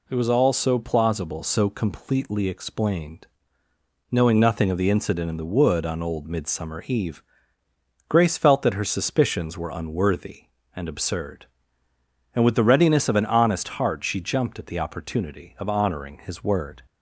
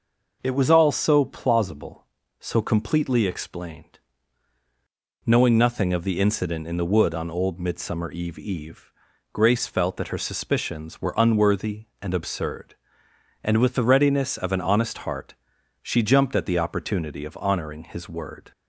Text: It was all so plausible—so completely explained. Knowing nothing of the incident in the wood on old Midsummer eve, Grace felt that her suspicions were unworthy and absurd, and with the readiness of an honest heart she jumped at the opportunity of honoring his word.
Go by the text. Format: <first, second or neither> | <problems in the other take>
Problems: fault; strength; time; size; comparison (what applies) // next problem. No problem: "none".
first | says "eve" twice; at 8.3 s // pauses between "heart" and "she"; noticeable; at 15.3 s; 0.48 s long